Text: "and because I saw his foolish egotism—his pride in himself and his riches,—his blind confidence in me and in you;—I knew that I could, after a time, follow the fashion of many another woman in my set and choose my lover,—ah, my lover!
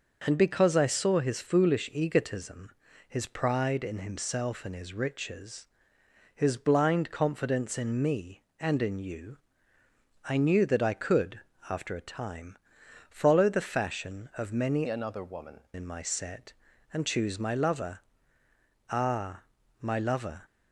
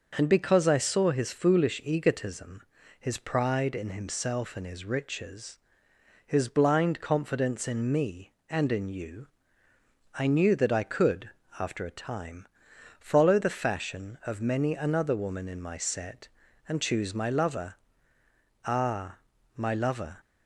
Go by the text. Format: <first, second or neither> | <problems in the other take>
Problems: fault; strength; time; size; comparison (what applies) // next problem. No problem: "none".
second | starts louder than the rest; noticeable; until 1.2 s; 6 dB // changes voice from "another" to "woman"; from 14.8 to 15.6 s; 0.8 s long